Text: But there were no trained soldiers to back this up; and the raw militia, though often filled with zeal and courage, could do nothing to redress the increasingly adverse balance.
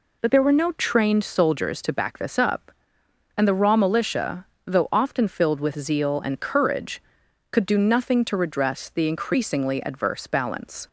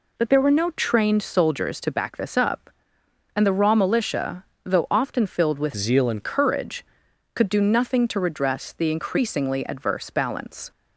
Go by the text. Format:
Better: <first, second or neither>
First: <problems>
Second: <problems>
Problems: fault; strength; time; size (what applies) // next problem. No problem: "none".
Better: first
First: none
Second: changes voice from "zeal" to "and"; from 5.7 to 6.2 s; 0.5 s long